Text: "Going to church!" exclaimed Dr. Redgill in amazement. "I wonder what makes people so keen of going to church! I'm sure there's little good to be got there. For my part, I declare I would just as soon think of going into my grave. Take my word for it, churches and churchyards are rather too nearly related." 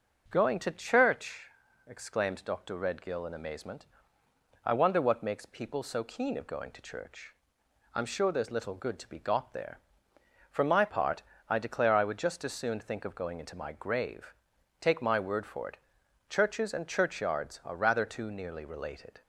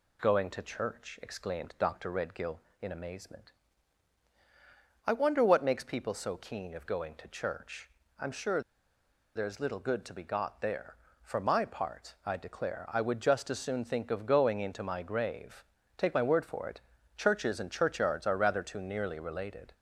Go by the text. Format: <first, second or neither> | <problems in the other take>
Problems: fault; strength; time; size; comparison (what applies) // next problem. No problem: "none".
first | pauses between "sure" and "there's"; noticeable; at 8.6 s; 0.75 s long